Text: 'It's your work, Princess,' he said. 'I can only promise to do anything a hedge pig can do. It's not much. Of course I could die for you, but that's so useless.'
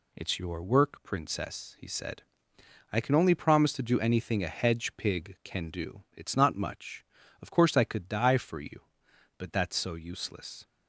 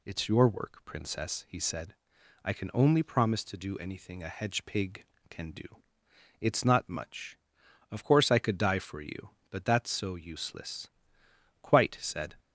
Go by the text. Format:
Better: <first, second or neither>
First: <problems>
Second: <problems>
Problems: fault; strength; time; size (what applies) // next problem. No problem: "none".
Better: first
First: none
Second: goes on to say "Quite said"; noticeable; from 11.6 s on; 0.72 s long